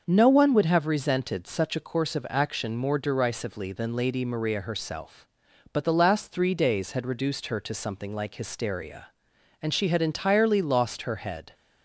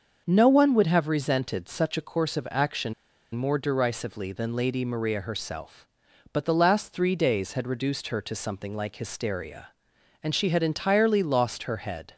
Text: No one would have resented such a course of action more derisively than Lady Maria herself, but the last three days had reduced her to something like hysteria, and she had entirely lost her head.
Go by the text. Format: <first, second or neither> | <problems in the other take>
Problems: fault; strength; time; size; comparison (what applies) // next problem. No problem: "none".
first | starts louder than the rest; until 1.2 s; 6.5 dB; also in the first // pauses between "action" and "more"; at 2.9 s; 0.40 s long